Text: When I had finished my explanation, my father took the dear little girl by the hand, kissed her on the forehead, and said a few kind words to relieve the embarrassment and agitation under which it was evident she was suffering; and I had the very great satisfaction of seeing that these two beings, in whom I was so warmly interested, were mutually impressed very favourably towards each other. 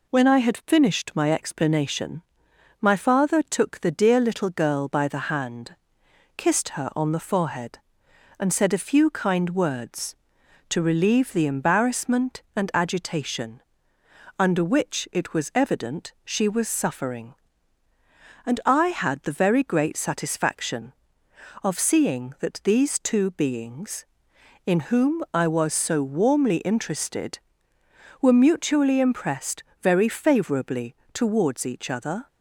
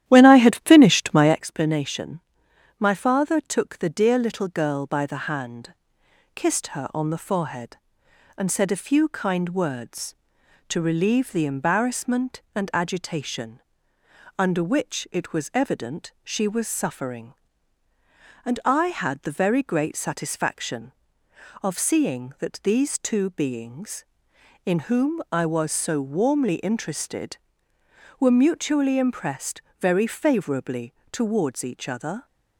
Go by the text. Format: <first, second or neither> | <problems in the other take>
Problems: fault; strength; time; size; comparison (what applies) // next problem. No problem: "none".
first | starts louder than the rest; strong; until 1.4 s; 12 dB // pauses between "agitation" and "under"; noticeable; at 13.5 s; 0.78 s long; noticeable in the first // pauses between "impressed" and "very"; slight; at 29.6 s; 0.18 s long; slight in the first // pauses between "favourably" and "towards"; slight; at 30.9 s; 0.18 s long; slight in the first